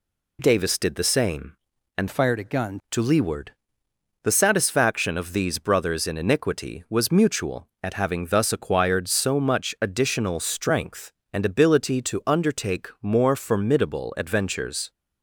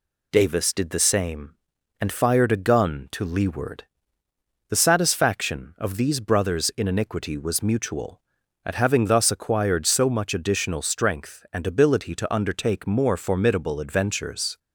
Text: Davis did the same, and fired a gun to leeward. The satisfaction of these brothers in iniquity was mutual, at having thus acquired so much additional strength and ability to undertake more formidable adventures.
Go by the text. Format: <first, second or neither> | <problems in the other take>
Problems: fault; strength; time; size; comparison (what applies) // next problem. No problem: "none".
second | changes voice from "fired" to "gun"; from 2.0 to 2.7 s; 0.7 s long